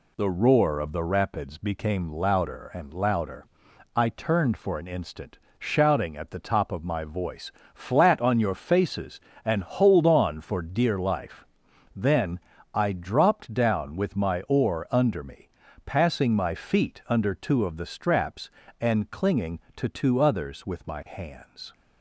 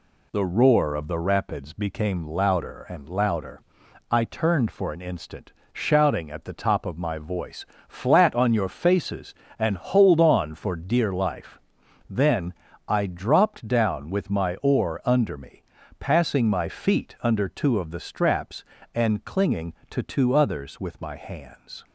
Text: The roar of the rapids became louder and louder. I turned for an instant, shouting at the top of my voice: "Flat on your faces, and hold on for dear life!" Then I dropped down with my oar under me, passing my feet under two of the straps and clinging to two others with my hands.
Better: neither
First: pauses between "Then" and "I"; slight; at 12.4 s; 0.34 s long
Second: pauses between "Then" and "I"; slight; at 12.5 s; 0.34 s long

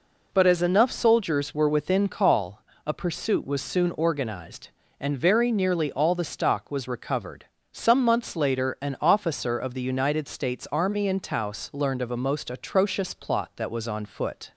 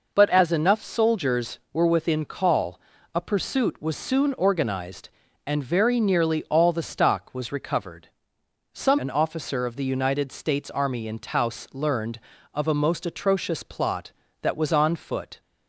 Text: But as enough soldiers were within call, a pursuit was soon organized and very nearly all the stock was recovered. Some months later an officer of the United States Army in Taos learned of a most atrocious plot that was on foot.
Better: first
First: none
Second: skips "months later"; at 8.9 s

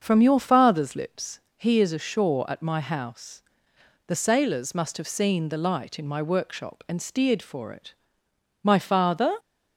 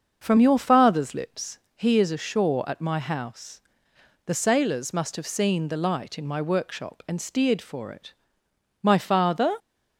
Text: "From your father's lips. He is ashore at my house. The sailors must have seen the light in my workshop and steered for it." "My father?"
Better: neither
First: starts louder than the rest; until 1.0 s; 6.5 dB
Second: starts louder than the rest; until 1.2 s; 6.5 dB

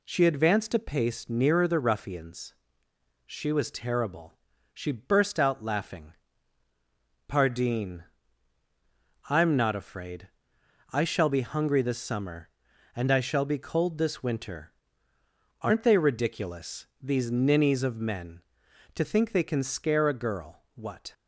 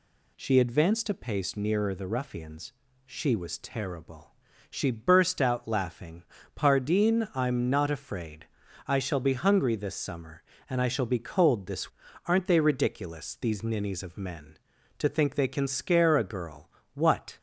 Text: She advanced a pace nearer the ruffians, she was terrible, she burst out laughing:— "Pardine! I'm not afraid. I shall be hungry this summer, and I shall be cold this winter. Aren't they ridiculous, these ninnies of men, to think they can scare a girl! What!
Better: first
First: none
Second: skips "winter"; at 12.0 s

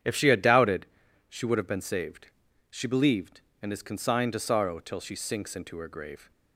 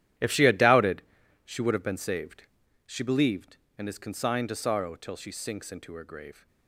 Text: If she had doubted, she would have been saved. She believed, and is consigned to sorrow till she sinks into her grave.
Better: first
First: starts louder than the rest; strong; until 1.4 s; 9 dB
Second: gets quieter; strong; throughout; 14 dB // starts louder than the rest; strong; until 1.6 s; 12 dB

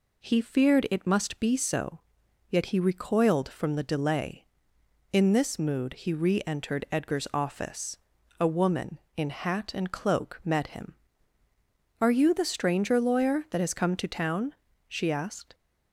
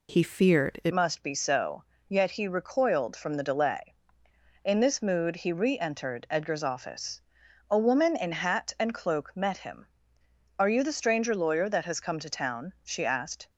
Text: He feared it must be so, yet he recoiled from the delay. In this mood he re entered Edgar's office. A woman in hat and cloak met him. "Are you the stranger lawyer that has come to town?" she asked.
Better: first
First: none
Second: changes voice at "must"; from 0.9 s on; 12.5 s long

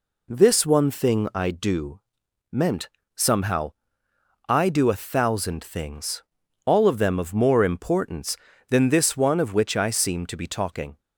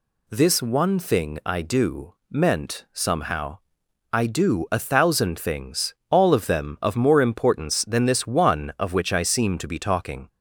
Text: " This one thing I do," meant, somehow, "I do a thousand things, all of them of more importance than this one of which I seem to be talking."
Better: neither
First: none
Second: none

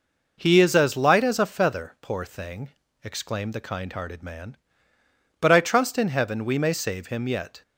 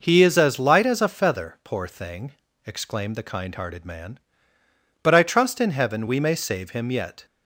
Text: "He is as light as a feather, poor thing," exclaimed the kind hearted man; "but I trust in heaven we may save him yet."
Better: neither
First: none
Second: none

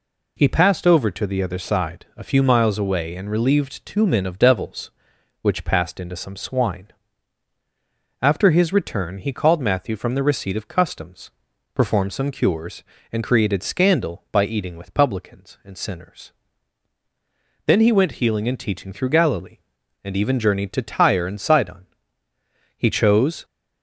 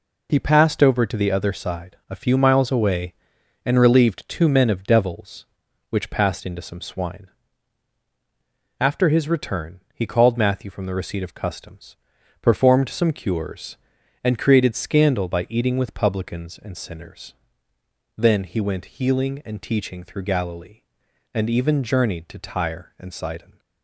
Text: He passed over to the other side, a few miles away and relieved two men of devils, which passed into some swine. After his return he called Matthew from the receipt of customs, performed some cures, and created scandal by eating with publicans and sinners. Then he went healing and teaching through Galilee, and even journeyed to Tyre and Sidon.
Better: second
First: goes on to say "He chose"; noticeable; from 22.7 s on; 0.68 s long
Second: none

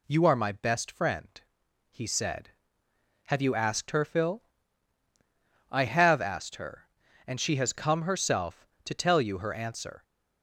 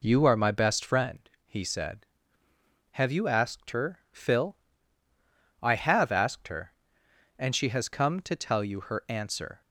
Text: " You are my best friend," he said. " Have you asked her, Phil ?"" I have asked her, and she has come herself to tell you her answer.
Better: first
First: none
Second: skips "herself"; at 8.2 s

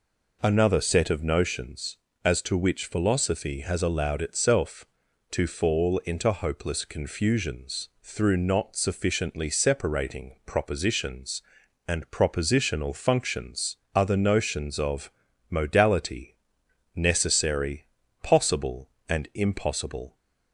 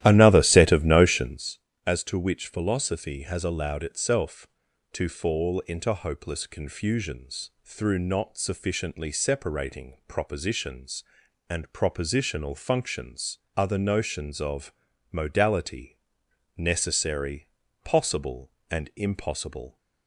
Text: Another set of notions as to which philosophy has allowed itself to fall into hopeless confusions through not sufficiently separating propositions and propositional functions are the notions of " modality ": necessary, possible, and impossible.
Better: first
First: none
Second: starts louder than the rest; strong; until 1.6 s; 13.5 dB

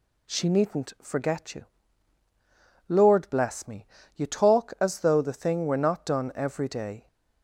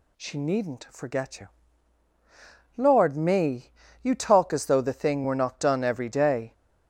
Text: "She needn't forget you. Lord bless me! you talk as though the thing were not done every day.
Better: first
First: none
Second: skips "bless"; at 3.1 s

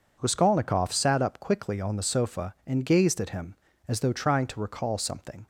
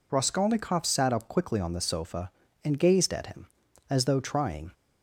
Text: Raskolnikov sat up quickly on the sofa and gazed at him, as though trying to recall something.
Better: first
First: none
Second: stops before "to recall something"; at 4.7 s

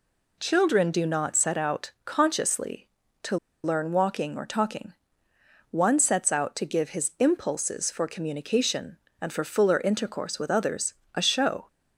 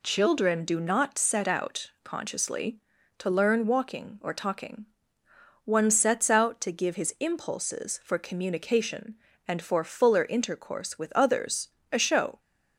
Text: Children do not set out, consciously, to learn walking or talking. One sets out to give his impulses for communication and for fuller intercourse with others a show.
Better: second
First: pauses between "to" and "learn"; slight; at 3.3 s; 0.28 s long // pauses between "others" and "a"; slight; at 10.9 s; 0.22 s long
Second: pauses between "others" and "a"; slight; at 11.6 s; 0.22 s long

